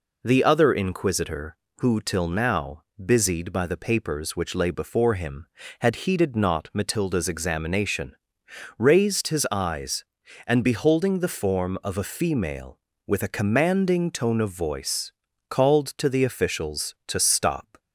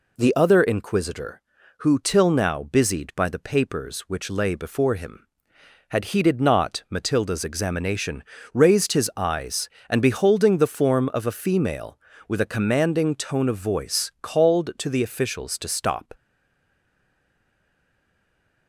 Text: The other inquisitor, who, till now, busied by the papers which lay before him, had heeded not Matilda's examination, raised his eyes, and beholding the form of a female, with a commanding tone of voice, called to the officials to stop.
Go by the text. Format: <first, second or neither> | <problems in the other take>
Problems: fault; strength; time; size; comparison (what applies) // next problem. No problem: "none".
first | stays silent after the last word; strong; from 16.1 s on; 2.5 s long